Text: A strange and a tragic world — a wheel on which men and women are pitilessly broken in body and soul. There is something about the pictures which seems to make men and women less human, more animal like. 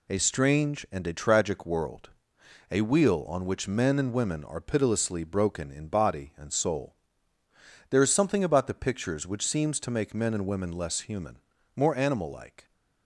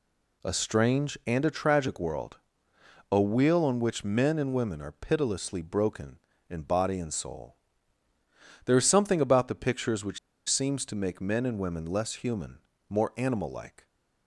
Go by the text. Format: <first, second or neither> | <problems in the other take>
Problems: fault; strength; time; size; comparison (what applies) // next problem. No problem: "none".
first | pauses between "which" and "seems"; slight; at 10.1 s; 0.30 s long